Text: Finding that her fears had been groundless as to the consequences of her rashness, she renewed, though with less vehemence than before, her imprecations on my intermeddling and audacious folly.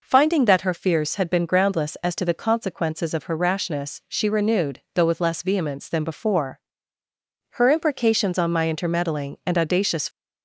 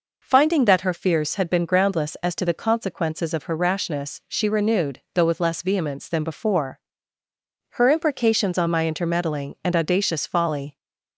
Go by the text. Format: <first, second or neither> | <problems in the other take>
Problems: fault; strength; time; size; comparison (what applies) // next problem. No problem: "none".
second | stops before "folly"; at 10.0 s